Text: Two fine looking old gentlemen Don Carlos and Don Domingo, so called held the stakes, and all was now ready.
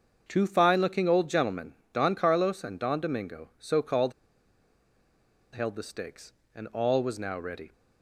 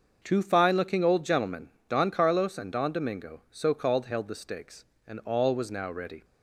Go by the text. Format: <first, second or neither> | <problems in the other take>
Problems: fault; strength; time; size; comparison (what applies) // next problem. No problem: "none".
second | starts louder than the rest; until 1.2 s; 6.5 dB; also in the second // pauses between "gentlemen" and "Don"; slight; at 1.7 s; 0.20 s long; slight in the second // pauses between "called" and "held"; strong; at 4.1 s; 1.4 s long